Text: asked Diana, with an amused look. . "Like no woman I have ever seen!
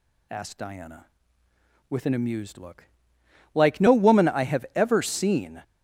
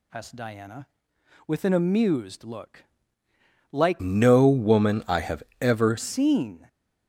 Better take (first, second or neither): first